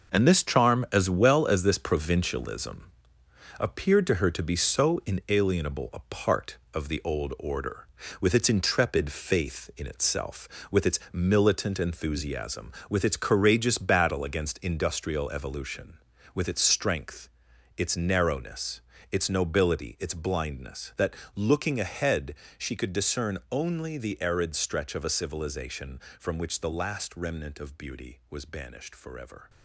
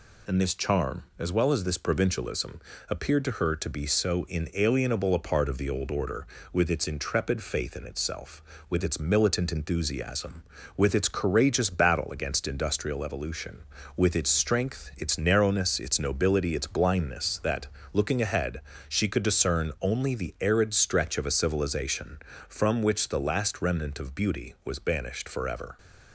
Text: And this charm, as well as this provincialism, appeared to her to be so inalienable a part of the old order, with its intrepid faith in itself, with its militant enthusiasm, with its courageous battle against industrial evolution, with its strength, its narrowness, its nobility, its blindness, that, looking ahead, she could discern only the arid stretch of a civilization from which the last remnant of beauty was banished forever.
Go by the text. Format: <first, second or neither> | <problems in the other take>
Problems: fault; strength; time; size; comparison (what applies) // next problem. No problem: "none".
second | gets quieter; strong; throughout; 8.5 dB